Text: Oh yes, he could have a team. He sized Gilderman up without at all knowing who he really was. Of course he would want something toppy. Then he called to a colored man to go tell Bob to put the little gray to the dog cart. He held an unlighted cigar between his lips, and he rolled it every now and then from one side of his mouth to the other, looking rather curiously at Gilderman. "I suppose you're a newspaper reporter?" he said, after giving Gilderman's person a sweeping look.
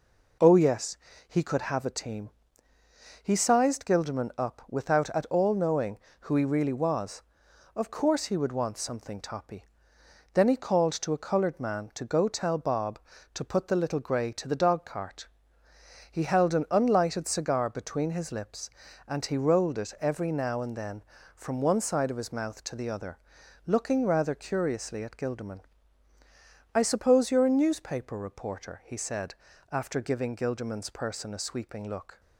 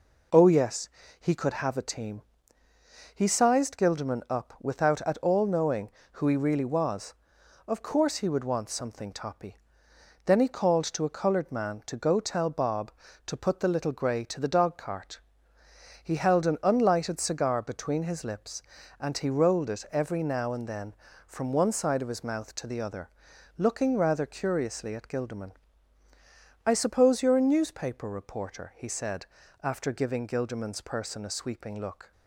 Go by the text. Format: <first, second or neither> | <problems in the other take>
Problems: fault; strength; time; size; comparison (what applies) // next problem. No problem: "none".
neither | none